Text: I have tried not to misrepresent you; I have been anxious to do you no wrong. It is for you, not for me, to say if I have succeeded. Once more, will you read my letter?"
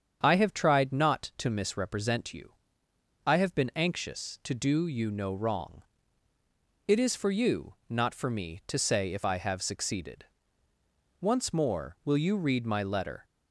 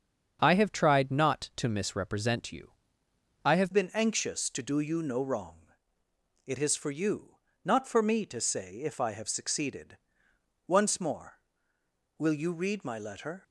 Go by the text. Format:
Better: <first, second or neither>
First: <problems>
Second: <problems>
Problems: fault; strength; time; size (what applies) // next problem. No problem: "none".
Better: first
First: starts louder than the rest; strong; until 1.2 s; 7.5 dB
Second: starts louder than the rest; strong; until 1.4 s; 7 dB // changes voice at "been"; from 3.7 s on; 9.7 s long